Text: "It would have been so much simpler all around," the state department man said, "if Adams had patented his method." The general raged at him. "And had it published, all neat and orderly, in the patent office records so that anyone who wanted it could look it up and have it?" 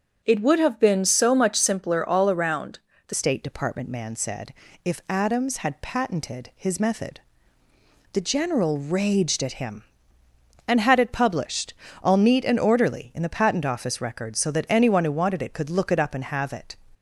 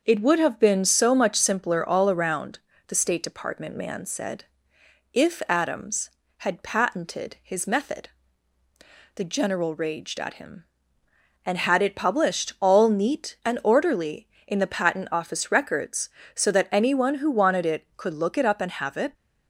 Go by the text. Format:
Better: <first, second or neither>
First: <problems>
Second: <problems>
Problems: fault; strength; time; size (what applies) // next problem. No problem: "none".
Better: second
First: starts louder than the rest; until 1.2 s; 7 dB // changes voice at "state"; from 3.1 s on; 13.6 s long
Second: starts louder than the rest; until 1.0 s; 6.5 dB